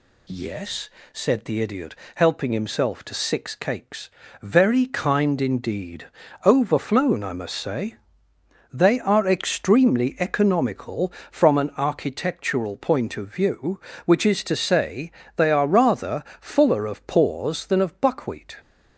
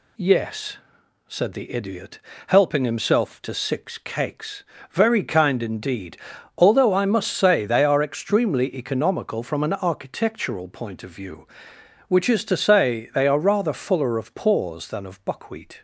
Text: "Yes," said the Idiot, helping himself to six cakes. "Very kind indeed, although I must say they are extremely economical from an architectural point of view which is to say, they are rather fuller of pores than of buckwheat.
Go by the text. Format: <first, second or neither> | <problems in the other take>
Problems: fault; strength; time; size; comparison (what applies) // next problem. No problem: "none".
second | says "overflown" for "although"; at 6.4 s // pauses between "say" and "they"; noticeable; at 7.9 s; 0.78 s long // pauses between "rather" and "fuller"; slight; at 16.2 s; 0.16 s long